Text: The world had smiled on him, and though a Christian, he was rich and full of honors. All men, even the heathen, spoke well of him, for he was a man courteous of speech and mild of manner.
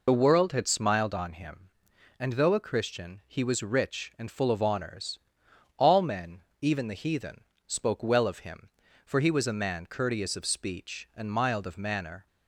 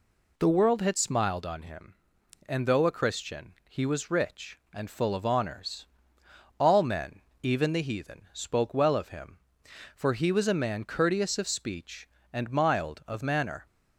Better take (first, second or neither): second